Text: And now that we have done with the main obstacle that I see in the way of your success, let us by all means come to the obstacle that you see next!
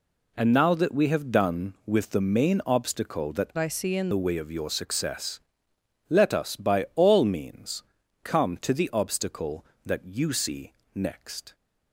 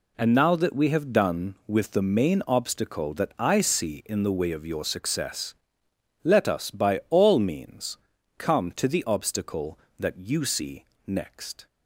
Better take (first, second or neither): second